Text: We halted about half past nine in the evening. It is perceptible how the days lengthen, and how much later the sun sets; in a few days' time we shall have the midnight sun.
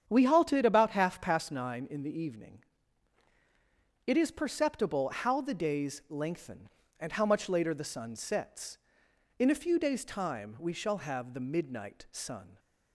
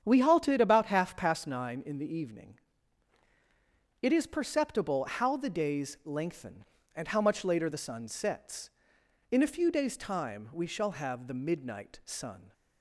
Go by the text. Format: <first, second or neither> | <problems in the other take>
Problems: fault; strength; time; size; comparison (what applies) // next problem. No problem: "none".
neither | starts louder than the rest; strong; the same in both